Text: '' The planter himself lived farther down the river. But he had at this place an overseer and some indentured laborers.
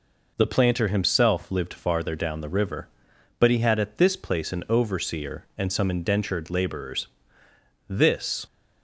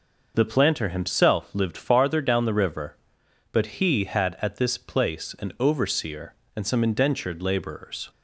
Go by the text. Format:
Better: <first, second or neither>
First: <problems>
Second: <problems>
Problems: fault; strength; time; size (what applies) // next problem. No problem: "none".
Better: second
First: goes on to say "This"; from 7.8 s on; 0.58 s long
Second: none